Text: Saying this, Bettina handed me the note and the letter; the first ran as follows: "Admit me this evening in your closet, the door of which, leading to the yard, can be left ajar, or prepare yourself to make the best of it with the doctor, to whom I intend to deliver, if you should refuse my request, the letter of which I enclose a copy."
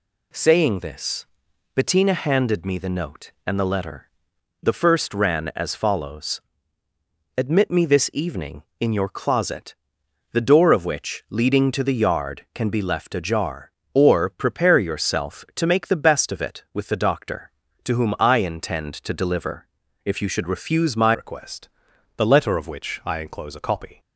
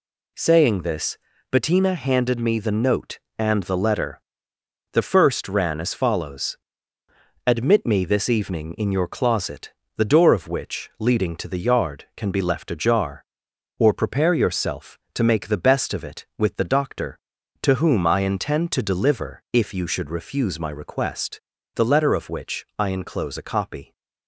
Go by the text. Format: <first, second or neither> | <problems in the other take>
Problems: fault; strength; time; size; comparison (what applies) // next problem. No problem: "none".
second | changes voice at "request"; from 21.1 s on; 2.8 s long